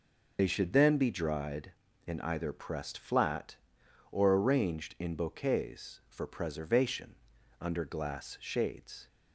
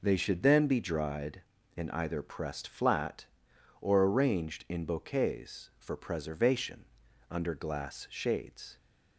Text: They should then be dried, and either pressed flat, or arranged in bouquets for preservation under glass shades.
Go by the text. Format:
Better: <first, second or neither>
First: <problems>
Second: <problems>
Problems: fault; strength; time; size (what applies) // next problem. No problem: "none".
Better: second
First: loses the start of "They"; at 0.3 s; 60 ms // pauses between "preservation" and "under"; at 7.1 s; 0.44 s long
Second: pauses between "preservation" and "under"; at 6.8 s; 0.44 s long